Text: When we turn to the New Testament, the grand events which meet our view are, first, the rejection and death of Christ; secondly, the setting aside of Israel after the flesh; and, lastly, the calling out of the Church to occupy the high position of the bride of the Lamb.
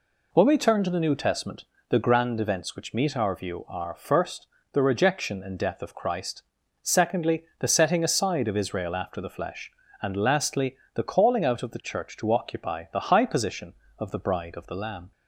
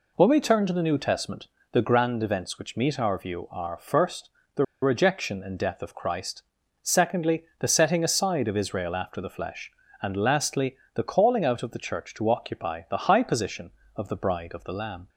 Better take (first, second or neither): first